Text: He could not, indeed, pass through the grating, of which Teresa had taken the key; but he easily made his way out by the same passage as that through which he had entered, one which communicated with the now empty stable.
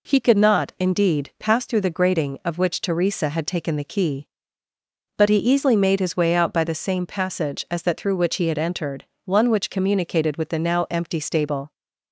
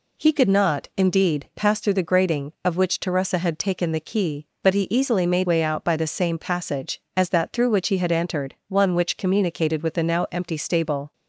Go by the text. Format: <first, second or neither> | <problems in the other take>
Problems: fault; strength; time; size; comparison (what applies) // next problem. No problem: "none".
first | skips "his"; at 5.4 s